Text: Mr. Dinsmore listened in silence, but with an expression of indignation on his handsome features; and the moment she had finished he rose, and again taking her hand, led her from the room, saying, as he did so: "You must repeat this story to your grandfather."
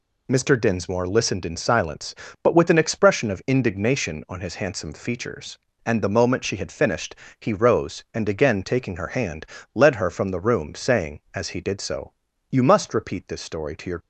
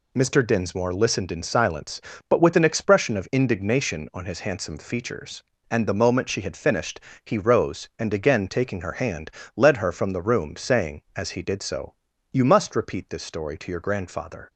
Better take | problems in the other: second | pauses between "finished" and "he"; slight; at 7.1 s; 0.24 s long; slight in the second // stops before "grandfather"; at 13.9 s

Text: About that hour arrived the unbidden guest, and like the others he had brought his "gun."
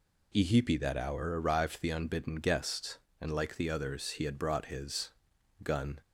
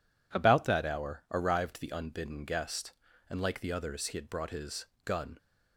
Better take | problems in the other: second | says "Ihipi" for "About"; at 0.3 s // pauses between "his" and "gun"; noticeable; at 5.1 s; 0.50 s long; slight in the second

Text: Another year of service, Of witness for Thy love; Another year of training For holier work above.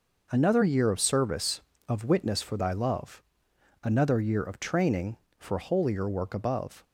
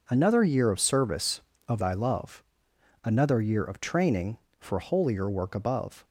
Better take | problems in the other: first | skips "witness for"; at 1.7 s

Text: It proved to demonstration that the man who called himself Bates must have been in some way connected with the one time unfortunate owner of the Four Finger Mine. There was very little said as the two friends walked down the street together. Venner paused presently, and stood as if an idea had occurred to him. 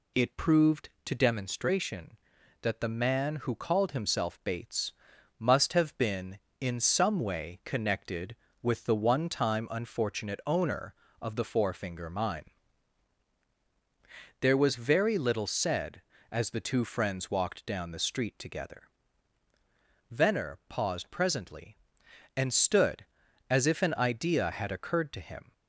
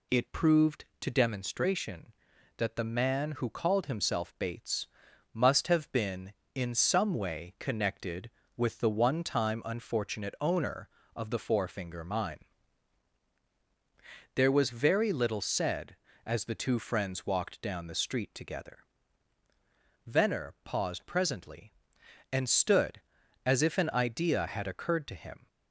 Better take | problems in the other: neither | pauses between "Bates" and "must"; noticeable; the same in both

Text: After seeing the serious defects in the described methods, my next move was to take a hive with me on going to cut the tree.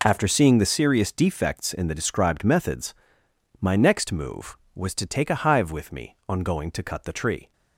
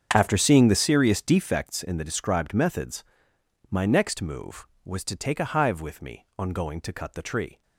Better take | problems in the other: first | starts louder than the rest; strong; until 1.6 s; 7.5 dB

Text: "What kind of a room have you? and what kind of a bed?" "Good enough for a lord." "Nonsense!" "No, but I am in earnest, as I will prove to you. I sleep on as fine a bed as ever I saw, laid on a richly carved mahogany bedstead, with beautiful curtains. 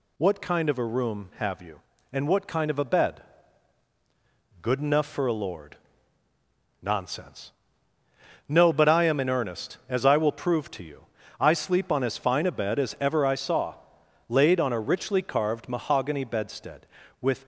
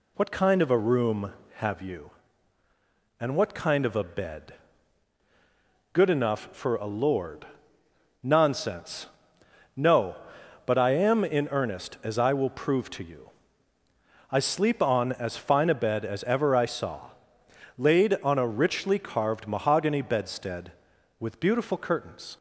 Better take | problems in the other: second | stops before "beautiful curtains"; at 17.4 s

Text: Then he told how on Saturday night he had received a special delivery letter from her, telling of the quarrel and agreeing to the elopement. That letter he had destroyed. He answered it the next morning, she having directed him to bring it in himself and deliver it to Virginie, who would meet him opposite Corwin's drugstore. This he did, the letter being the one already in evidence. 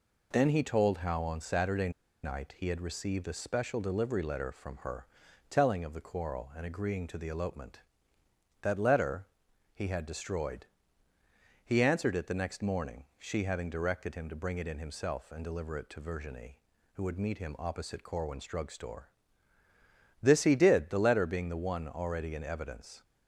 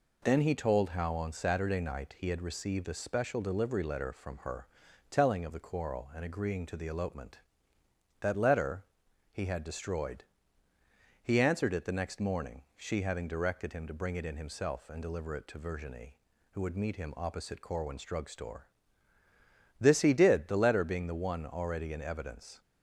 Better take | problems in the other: second | pauses between "Saturday" and "night"; slight; at 1.8 s; 0.34 s long // pauses between "letter" and "he"; noticeable; at 9.2 s; 0.48 s long; noticeable in the second

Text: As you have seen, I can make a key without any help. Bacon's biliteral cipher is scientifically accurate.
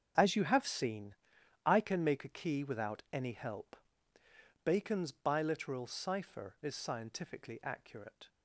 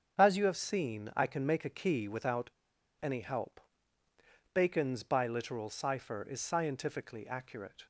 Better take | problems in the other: first | starts louder than the rest; strong; until 1.2 s; 7.5 dB; strong in the first // pauses between "without" and "any"; noticeable; at 2.4 s; 0.52 s long

